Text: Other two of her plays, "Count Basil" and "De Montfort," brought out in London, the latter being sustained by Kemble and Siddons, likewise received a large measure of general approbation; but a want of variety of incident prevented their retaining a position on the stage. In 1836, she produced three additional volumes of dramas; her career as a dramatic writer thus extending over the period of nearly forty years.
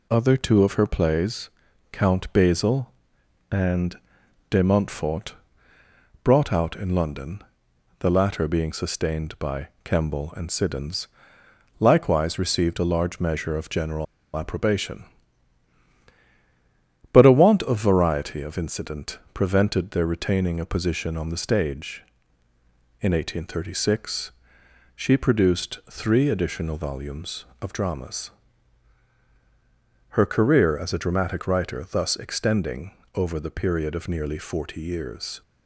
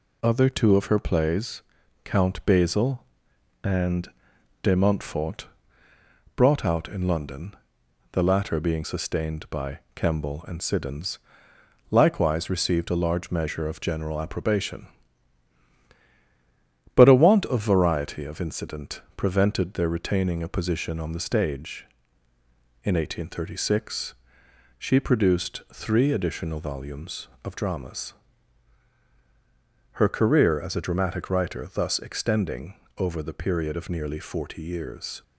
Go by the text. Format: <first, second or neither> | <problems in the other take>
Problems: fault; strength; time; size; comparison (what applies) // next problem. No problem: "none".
second | pauses between "and" and "De"; noticeable; at 3.9 s; 0.52 s long; noticeable in the second // pauses between "general" and "approbation"; slight; at 14.0 s; 0.30 s long // pauses between "extending" and "over"; slight; at 32.9 s; 0.24 s long; slight in the second